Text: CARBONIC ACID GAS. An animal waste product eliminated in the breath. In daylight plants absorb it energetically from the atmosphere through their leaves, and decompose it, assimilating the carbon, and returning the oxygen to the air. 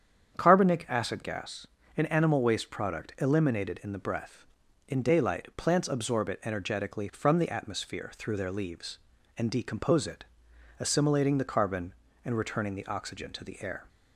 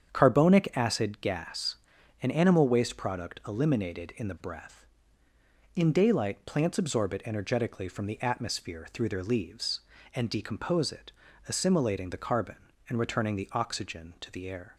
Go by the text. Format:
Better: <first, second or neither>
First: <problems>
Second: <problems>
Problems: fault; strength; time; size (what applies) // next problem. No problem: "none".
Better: neither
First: starts louder than the rest; strong; until 1.4 s; 8.5 dB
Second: starts louder than the rest; strong; until 1.1 s; 8 dB